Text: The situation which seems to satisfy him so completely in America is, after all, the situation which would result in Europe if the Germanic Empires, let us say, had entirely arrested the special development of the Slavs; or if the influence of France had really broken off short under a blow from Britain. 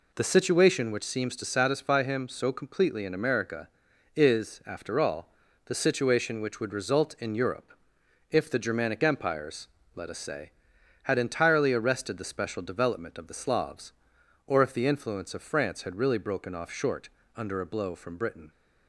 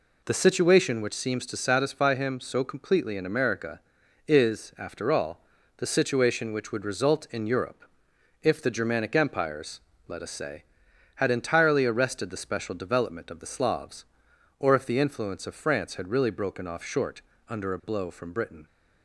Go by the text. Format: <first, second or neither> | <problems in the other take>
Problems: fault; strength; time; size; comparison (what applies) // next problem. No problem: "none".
neither | pauses between "Europe" and "if"; noticeable; the same in both // pauses between "short" and "under"; slight; the same in both